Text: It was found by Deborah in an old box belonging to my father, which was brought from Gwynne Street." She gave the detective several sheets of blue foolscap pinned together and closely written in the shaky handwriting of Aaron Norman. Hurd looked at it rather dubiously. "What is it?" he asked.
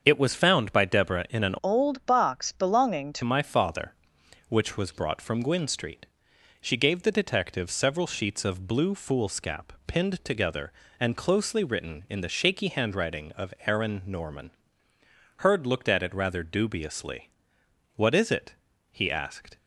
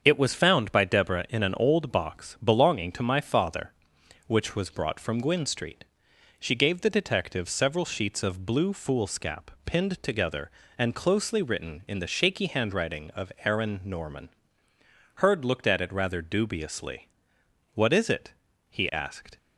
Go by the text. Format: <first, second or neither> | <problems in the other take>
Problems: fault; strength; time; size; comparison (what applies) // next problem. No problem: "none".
second | starts louder than the rest; until 1.0 s; 7 dB; also in the second // changes voice from "old" to "to"; from 1.6 to 3.2 s; 1.6 s long